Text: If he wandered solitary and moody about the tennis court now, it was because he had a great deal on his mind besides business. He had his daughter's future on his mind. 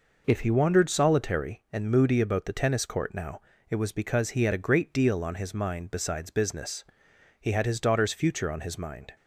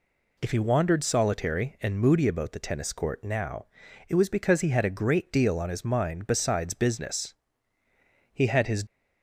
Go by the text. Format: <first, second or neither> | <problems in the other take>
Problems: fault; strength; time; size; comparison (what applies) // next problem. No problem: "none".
first | stops before "daughter's future on his mind"; at 8.8 s